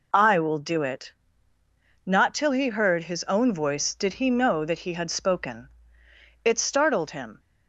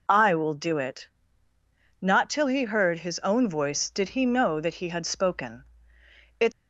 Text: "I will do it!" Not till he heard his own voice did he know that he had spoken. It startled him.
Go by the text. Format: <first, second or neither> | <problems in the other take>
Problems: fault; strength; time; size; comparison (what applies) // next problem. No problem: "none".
first | stops before "startled him"; at 6.5 s